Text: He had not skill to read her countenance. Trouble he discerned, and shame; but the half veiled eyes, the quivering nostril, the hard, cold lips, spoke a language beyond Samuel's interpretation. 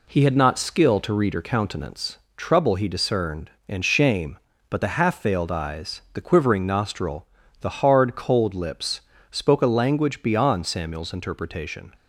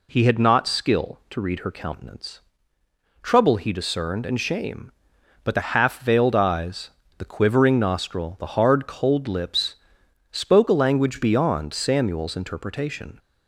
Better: neither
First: none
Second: none

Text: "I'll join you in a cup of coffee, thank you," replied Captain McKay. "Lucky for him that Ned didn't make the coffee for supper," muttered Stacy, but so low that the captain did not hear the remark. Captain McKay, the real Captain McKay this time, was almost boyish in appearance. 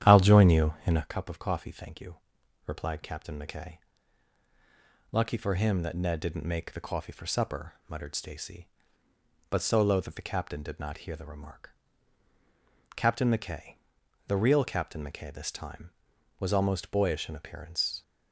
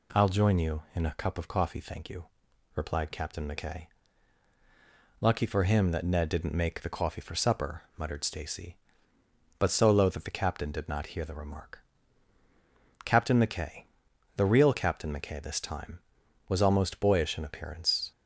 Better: second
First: starts louder than the rest; strong; until 1.1 s; 10 dB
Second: none

